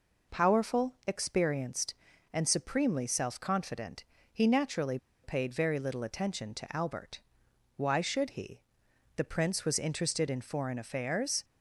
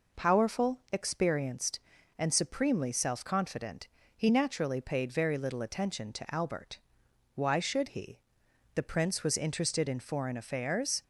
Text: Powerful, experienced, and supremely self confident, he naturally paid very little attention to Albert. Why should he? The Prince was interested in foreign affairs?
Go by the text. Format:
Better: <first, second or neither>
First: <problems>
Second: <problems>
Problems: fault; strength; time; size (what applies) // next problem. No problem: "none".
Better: second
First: pauses between "naturally" and "paid"; slight; at 4.9 s; 0.25 s long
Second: none